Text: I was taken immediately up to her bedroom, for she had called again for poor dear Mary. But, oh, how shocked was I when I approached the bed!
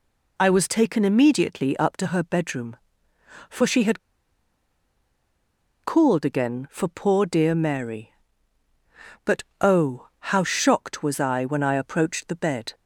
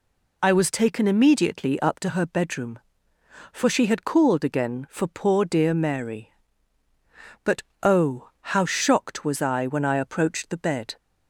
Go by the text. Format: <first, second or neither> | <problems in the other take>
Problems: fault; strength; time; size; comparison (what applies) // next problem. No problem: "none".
second | pauses between "had" and "called"; strong; at 3.9 s; 1.8 s long